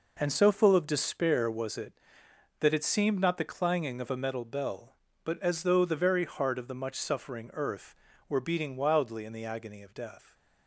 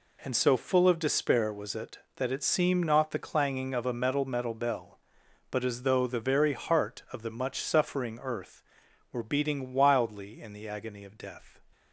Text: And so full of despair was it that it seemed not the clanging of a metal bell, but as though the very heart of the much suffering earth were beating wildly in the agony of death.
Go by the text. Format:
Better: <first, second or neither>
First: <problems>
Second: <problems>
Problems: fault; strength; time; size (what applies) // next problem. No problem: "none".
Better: first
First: none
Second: says "metal" twice; at 4.2 s